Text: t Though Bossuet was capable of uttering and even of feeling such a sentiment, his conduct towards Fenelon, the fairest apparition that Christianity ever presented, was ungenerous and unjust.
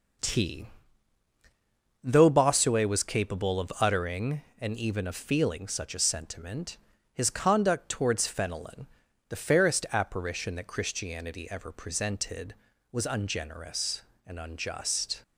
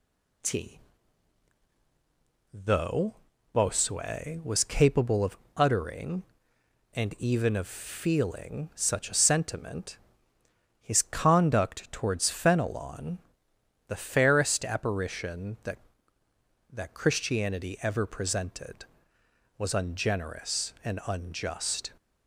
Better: first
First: pauses between "t" and "Though"; strong; at 0.6 s; 1.3 s long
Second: pauses between "t" and "Though"; strong; at 0.7 s; 1.7 s long // pauses between "Though" and "Bossuet"; at 3.1 s; 0.38 s long // pauses between "of" and "uttering"; slight; at 5.3 s; 0.20 s long // says "that" twice; at 16.7 s

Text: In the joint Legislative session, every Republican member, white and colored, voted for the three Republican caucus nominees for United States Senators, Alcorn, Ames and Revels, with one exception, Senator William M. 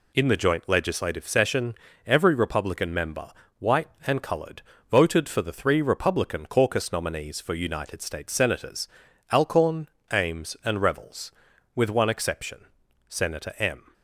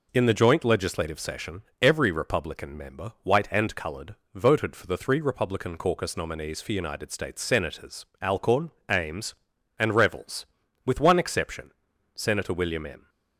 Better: second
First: skips "William"; at 13.5 s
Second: none

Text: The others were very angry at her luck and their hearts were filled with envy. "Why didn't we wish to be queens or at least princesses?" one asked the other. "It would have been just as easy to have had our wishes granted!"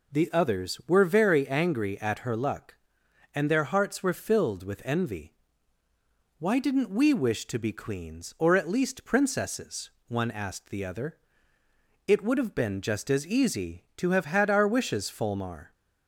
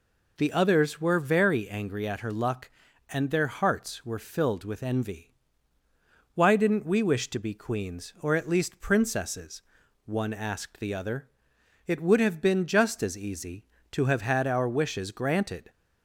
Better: second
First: says "fulmar" for "granted"; at 15.1 s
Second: none

